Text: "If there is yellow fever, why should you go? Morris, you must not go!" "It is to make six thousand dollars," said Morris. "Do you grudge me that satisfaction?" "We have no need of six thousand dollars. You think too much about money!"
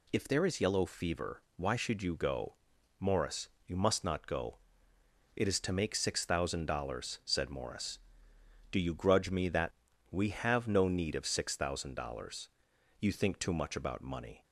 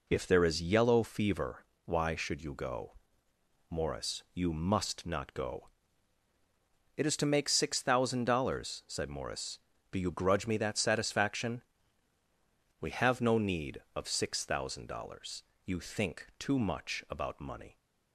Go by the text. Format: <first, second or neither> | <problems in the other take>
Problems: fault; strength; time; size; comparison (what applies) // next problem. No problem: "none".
second | skips "satisfaction"; at 9.9 s